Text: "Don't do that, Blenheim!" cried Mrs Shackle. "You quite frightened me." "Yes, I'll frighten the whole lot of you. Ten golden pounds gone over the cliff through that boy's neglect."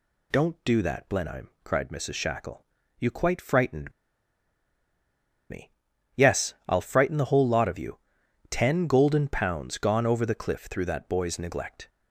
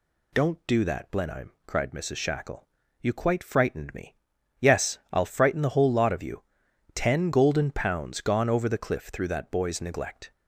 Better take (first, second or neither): second